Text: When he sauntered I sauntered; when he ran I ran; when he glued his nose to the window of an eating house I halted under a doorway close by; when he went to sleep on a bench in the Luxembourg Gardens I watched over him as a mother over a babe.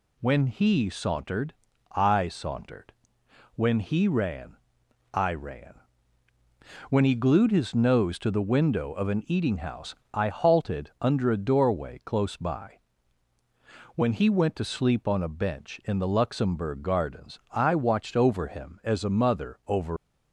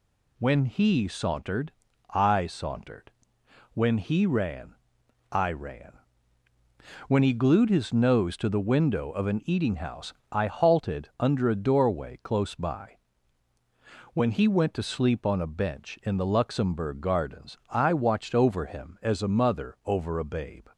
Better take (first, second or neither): second